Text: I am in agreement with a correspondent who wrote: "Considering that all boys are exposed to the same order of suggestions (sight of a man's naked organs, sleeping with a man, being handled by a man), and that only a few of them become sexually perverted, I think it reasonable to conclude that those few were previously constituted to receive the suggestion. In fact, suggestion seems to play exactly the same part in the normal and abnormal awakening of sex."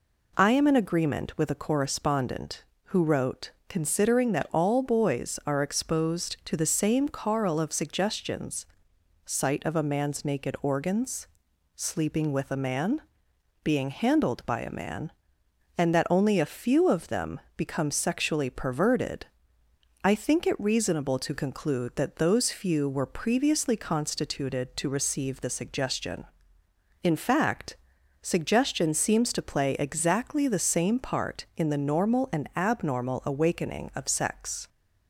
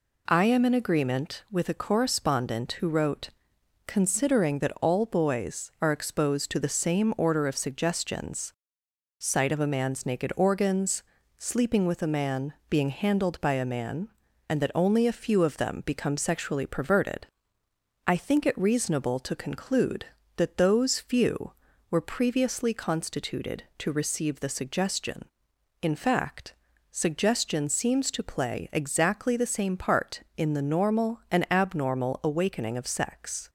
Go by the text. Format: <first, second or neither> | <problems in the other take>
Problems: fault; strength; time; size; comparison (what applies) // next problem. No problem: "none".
second | says "carl" for "order"; at 7.0 s // pauses between "them" and "become"; slight; at 17.3 s; 0.18 s long